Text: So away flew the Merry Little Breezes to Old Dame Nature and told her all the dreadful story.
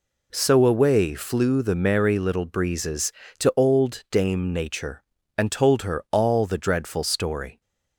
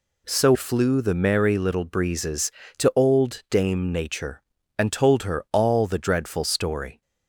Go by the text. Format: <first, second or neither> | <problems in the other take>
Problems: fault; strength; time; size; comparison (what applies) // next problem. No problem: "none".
first | skips "away"; at 0.5 s